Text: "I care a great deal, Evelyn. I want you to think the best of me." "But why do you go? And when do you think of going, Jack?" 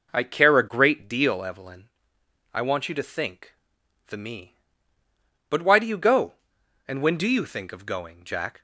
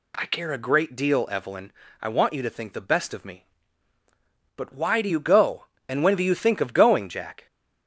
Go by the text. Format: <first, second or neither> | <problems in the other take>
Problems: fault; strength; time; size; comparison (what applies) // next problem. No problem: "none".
second | pauses between "think" and "the"; noticeable; at 3.5 s; 0.54 s long // skips "best of"; at 4.1 s